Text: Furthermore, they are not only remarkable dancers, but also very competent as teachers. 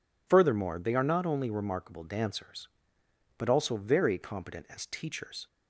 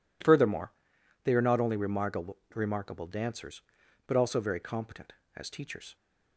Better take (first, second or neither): first